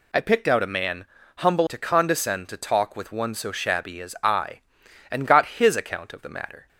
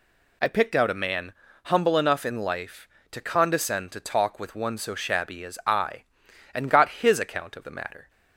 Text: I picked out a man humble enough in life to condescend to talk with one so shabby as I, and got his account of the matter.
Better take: second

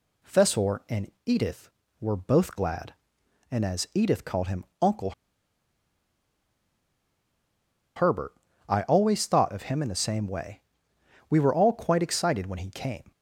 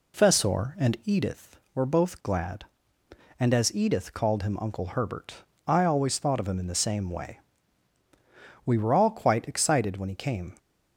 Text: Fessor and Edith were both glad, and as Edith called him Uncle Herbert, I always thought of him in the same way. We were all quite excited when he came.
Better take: second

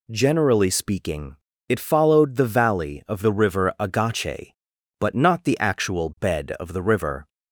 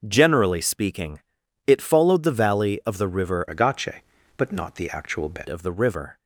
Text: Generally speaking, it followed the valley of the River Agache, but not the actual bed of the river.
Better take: first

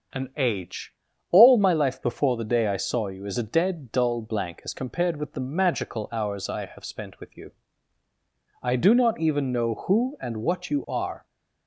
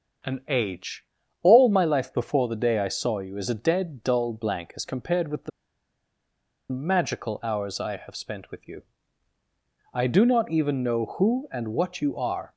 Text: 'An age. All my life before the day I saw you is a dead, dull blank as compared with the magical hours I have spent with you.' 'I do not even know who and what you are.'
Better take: first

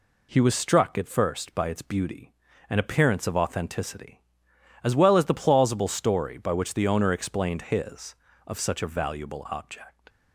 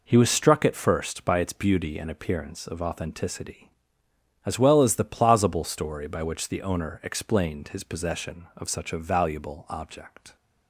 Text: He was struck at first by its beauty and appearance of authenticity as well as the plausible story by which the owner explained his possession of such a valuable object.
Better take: second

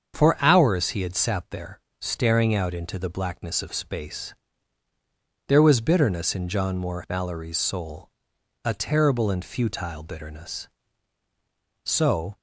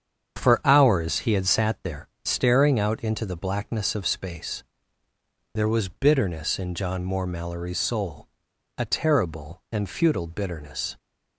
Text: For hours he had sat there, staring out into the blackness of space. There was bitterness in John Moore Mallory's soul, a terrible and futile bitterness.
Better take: second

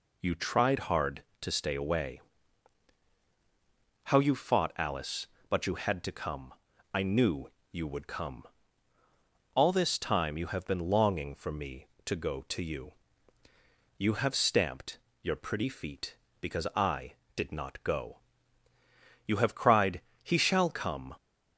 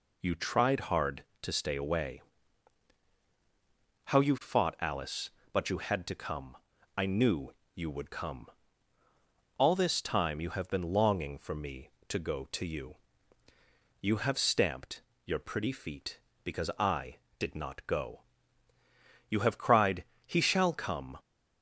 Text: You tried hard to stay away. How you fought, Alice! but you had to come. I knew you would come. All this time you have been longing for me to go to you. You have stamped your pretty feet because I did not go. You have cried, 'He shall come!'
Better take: neither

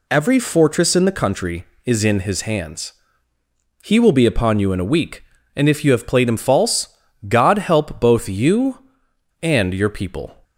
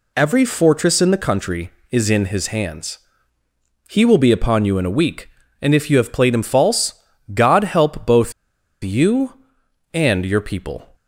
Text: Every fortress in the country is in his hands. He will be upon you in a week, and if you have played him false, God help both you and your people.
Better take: first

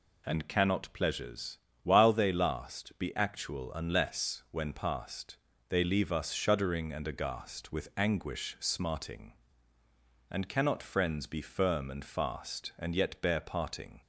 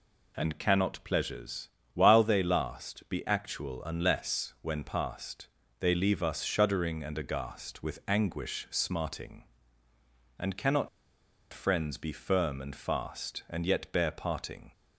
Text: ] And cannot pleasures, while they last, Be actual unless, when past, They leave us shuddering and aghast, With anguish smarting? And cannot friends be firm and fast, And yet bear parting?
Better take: first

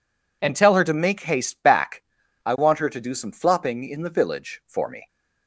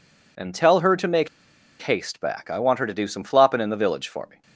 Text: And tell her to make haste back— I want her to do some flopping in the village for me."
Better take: first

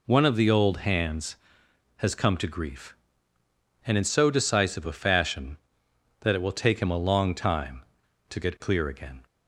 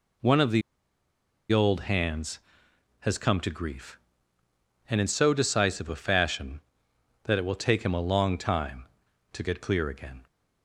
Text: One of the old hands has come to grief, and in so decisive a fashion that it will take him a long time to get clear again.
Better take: first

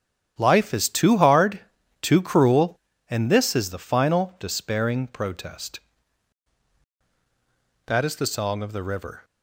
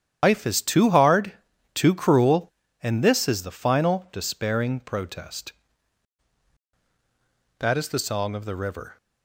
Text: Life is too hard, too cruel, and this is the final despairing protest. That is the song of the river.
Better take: first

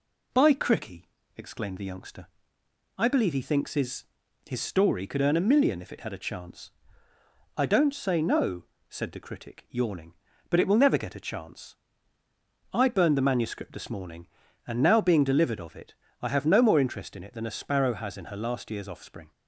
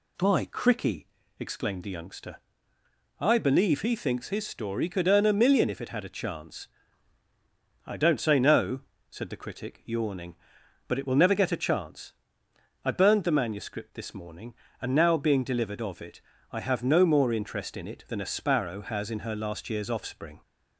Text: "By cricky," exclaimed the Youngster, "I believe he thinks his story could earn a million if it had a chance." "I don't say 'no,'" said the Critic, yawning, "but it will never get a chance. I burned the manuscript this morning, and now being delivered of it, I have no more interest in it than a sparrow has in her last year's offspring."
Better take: second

